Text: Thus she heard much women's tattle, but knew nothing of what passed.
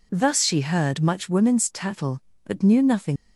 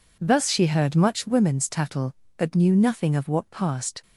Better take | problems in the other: second | stops before "of what passed"; at 3.1 s

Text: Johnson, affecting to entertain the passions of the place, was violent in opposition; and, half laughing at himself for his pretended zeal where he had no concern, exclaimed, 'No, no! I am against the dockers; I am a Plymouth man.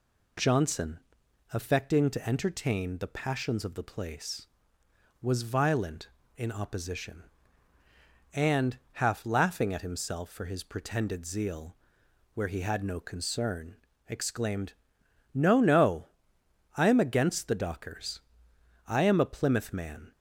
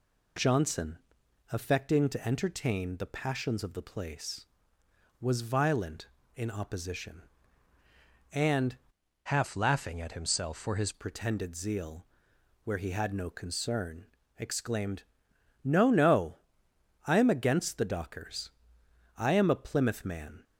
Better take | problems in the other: first | changes voice from "half" to "his"; from 9.2 to 10.9 s; 1.7 s long // pauses between "zeal" and "where"; noticeable; at 12.0 s; 0.60 s long; noticeable in the first

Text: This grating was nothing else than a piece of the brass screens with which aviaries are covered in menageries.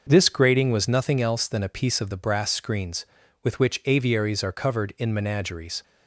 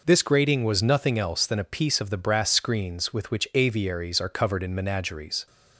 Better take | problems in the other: neither | none

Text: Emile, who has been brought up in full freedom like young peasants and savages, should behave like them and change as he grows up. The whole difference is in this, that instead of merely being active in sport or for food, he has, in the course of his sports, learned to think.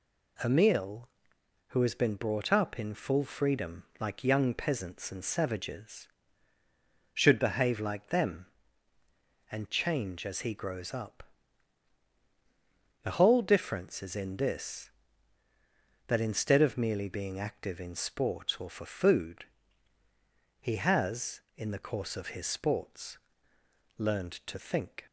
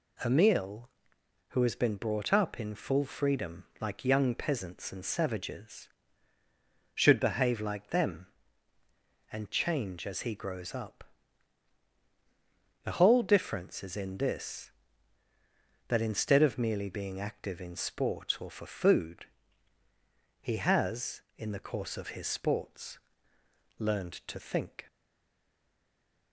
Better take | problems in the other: first | pauses between "freedom" and "like"; slight; at 3.6 s; 0.16 s long; slight in the first // stays silent after the last word; noticeable; from 24.8 s on; 1.5 s long

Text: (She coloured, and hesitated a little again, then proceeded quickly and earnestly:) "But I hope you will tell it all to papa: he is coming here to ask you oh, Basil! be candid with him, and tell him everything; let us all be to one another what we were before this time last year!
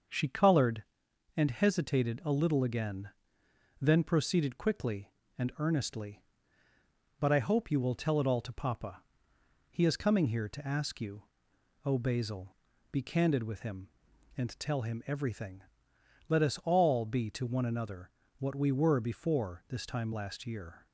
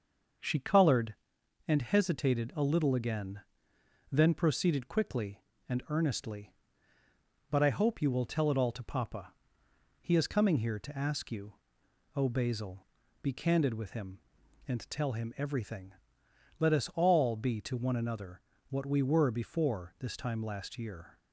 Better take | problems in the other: neither | starts louder than the rest; the same in both // pauses between "you" and "oh"; noticeable; the same in both // pauses between "another" and "what"; slight; the same in both

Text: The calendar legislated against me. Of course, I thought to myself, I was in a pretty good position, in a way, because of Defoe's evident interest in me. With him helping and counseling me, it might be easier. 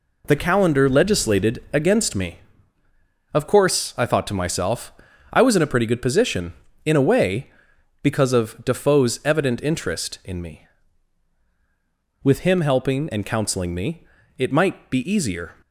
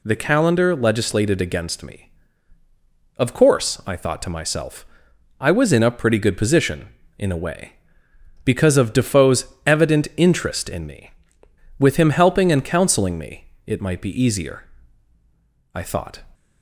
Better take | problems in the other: first | pauses between "Defoe's" and "evident"; slight; at 9.4 s; 0.20 s long // goes on to say "I thought"; from 15.7 s on; 0.50 s long

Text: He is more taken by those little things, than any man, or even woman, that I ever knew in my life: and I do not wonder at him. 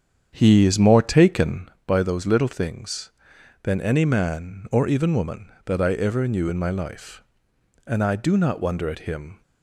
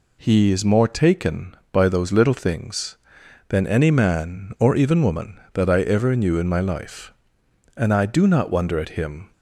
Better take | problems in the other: second | starts louder than the rest; strong; until 1.8 s; 8 dB

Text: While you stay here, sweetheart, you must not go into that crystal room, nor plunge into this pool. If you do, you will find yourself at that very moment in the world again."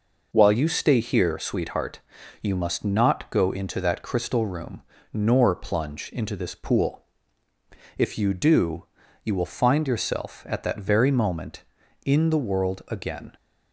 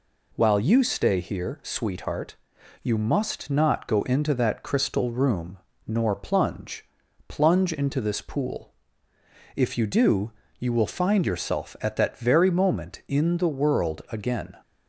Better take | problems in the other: first | says "plunge" twice; at 7.2 s

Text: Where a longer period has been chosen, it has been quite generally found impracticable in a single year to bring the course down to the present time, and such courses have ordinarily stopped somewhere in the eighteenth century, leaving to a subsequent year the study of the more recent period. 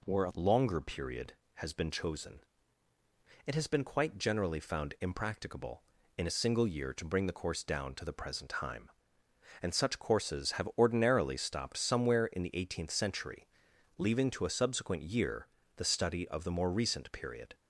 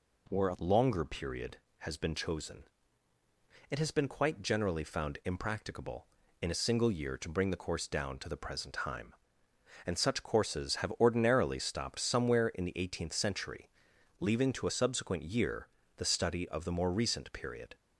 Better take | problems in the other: neither | pauses between "year" and "the"; slight; the same in both

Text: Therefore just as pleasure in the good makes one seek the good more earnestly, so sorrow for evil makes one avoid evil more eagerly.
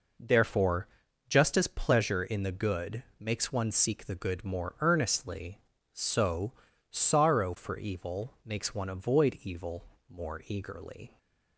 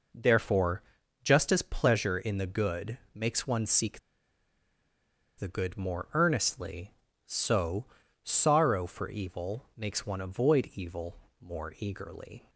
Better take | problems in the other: first | pauses between "Therefore" and "just"; at 0.8 s; 0.42 s long; also in the first // pauses between "good" and "makes"; slight; at 2.9 s; 0.16 s long; slight in the first // pauses between "seek" and "the"; strong; at 3.9 s; 1.3 s long // pauses between "so" and "sorrow"; slight; at 7.8 s; 0.36 s long; slight in the first // pauses between "evil" and "more"; slight; at 11.1 s; 0.24 s long; slight in the first

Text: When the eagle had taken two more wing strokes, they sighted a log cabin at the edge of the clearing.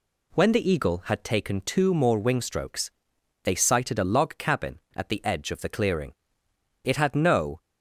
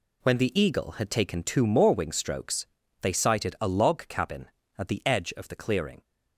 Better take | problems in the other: second | goes on to say "It had no"; noticeable; from 6.8 s on; 0.76 s long

